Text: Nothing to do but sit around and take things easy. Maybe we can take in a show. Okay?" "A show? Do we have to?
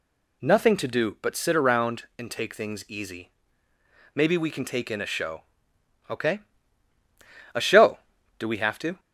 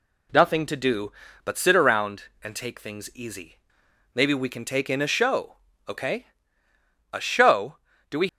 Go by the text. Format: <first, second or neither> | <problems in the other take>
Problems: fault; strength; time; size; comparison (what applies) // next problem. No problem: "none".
first | stops before "have to"; at 8.2 s